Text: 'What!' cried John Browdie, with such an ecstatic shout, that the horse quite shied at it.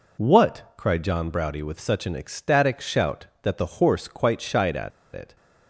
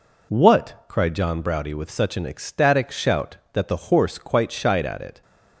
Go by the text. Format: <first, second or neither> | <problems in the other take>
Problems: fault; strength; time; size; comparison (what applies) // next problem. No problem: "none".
second | pauses between "at" and "it"; slight; at 4.9 s; 0.22 s long